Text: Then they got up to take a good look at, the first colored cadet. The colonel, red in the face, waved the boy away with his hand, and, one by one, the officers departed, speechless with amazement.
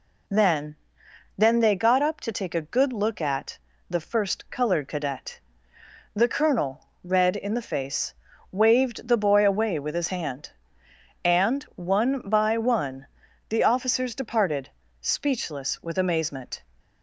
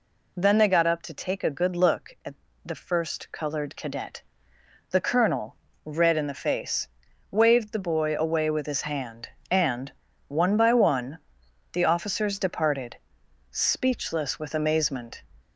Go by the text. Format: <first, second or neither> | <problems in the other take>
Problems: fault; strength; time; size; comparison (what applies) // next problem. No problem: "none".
second | says "Then" twice; at 1.3 s